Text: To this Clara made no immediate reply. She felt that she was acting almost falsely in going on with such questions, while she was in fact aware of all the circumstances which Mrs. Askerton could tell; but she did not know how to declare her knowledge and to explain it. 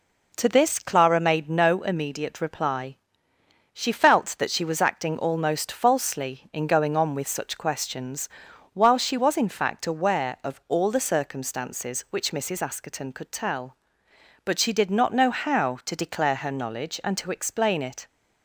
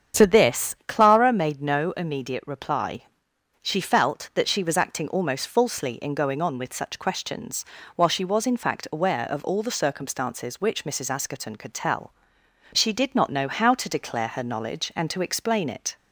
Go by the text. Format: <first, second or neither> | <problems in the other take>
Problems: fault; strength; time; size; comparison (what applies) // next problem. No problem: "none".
first | starts louder than the rest; strong; until 1.2 s; 8 dB // skips "but"; at 12.4 s